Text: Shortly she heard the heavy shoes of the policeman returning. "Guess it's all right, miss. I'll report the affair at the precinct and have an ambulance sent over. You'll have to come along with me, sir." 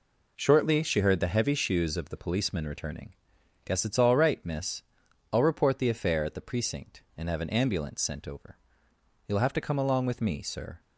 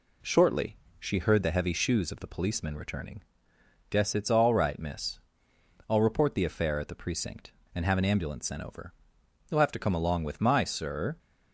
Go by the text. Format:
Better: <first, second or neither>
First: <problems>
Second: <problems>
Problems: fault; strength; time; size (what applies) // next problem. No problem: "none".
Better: first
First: none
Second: pauses between "Shortly" and "she"; slight; at 0.7 s; 0.22 s long // says "my" for "me"; at 10.3 s